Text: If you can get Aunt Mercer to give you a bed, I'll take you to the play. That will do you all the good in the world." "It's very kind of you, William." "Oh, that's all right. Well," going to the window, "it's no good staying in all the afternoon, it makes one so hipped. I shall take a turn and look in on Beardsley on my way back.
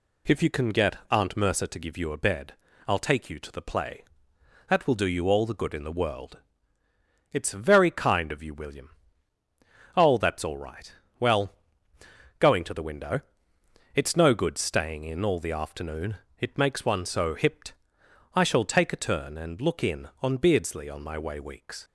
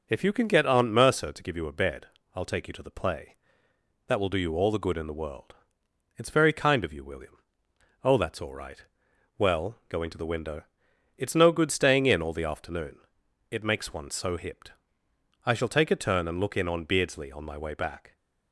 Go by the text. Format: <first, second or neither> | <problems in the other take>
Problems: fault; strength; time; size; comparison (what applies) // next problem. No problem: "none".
second | says "weeks" for "back"; at 21.3 s